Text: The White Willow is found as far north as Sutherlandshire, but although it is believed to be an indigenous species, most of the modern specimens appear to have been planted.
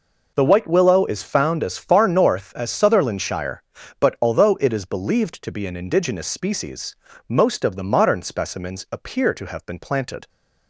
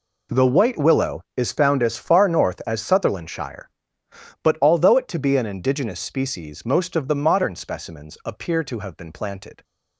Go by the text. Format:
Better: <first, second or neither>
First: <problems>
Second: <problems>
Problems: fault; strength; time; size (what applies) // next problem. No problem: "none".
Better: first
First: none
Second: skips "is believed"; at 5.0 s